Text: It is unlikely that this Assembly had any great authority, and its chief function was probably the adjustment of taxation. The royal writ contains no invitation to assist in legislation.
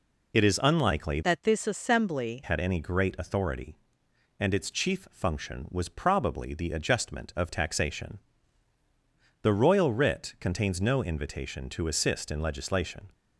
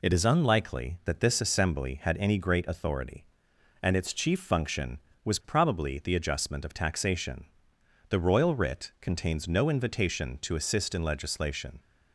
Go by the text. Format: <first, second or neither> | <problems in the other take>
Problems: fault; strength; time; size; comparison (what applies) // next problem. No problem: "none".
second | changes voice from "that" to "Assembly"; from 1.2 to 2.4 s; 1.2 s long